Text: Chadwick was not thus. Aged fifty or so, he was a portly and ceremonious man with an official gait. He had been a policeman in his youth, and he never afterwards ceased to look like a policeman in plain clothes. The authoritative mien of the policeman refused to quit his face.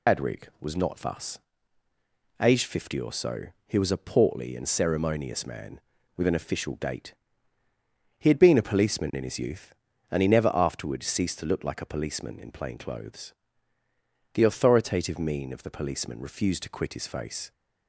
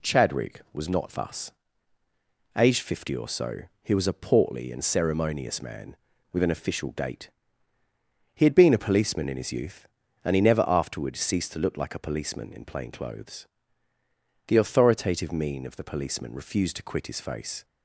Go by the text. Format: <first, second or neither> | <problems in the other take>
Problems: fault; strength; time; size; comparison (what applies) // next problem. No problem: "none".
second | loses the start of "Chadwick"; at 0.0 s; 180 ms